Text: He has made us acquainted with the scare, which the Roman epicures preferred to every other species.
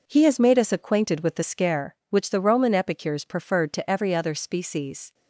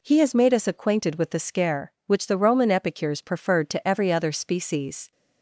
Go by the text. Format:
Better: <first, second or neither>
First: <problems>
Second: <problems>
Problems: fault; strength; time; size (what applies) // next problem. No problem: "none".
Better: second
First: gets quieter; strong; throughout; 9 dB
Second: none